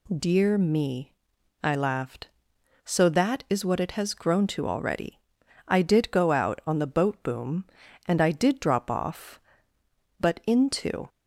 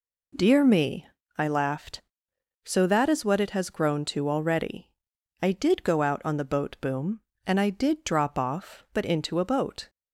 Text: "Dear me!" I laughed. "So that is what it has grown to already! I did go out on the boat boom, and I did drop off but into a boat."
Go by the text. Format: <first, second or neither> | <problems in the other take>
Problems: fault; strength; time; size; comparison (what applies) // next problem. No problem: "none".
second | stops before "a boat"; at 11.0 s